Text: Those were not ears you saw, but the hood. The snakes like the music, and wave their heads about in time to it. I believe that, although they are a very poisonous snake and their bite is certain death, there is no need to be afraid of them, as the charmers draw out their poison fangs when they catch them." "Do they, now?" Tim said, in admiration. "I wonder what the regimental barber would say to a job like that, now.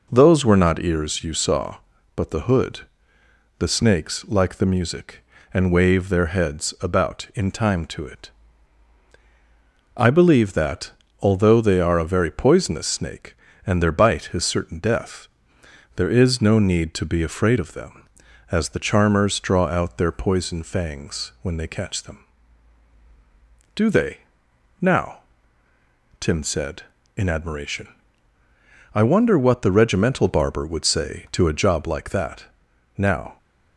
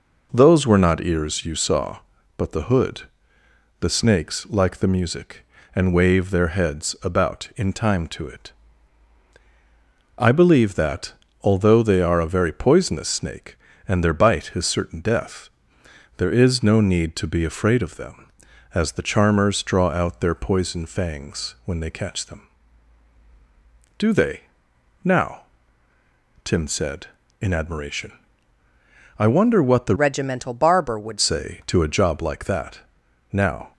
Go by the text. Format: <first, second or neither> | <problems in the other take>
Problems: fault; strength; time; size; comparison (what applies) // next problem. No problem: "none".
first | changes voice from "regimental" to "would"; from 29.9 to 31.1 s; 1.2 s long